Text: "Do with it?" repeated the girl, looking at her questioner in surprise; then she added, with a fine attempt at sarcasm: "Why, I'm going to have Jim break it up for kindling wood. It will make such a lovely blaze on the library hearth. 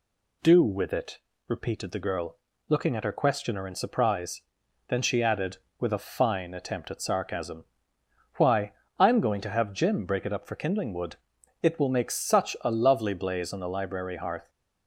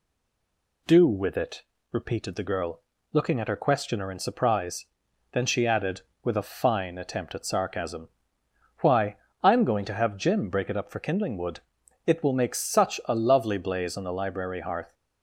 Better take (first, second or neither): first